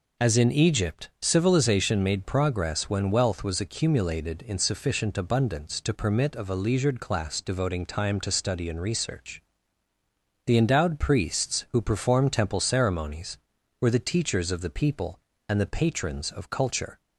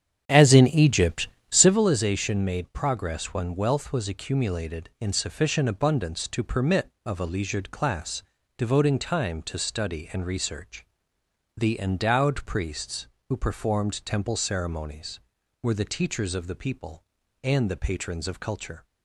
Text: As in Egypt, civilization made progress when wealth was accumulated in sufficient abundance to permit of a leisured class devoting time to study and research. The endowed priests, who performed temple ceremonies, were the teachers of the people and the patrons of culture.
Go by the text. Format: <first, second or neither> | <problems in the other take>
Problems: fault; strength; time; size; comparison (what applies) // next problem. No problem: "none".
first | starts louder than the rest; strong; until 1.8 s; 8.5 dB // pauses between "class" and "devoting"; slight; at 8.2 s; 0.34 s long